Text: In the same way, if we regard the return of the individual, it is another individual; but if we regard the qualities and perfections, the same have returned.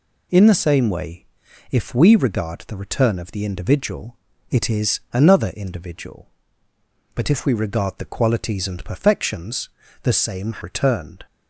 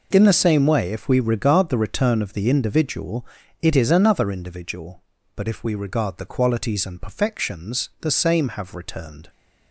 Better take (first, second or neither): second